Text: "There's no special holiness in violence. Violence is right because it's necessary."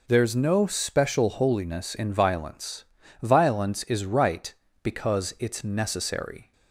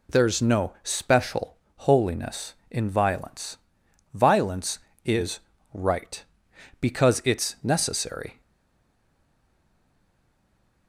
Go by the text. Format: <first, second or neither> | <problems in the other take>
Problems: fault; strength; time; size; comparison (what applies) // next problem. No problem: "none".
first | pauses between "special" and "holiness"; slight; at 1.5 s; 0.20 s long // pauses between "is" and "right"; slight; at 5.3 s; 0.34 s long // stays silent after the last word; strong; from 8.4 s on; 2.4 s long